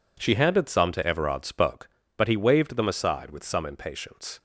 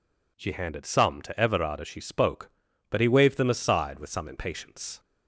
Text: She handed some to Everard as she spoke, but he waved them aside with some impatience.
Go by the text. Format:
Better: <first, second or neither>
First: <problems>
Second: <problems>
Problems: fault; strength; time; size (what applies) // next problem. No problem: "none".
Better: second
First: skips "as she"; at 1.4 s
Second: none